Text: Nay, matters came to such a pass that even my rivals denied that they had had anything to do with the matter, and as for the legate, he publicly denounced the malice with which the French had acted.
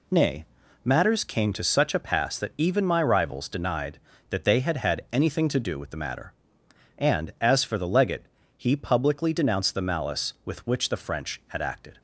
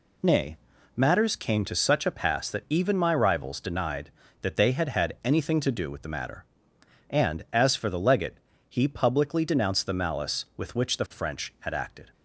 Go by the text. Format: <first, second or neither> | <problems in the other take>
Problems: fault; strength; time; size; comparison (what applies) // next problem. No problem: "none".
neither | none